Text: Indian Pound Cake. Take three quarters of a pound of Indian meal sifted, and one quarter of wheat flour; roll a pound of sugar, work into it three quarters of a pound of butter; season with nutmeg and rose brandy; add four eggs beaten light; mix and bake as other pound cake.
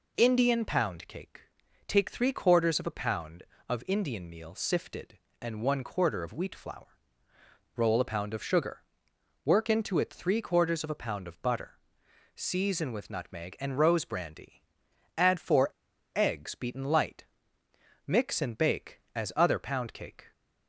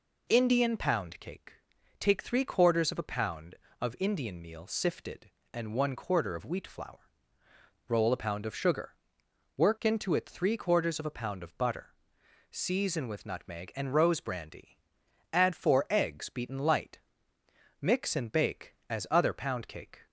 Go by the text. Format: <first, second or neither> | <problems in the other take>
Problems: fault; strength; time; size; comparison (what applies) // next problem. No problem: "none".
second | pauses between "four" and "eggs"; at 15.7 s; 0.45 s long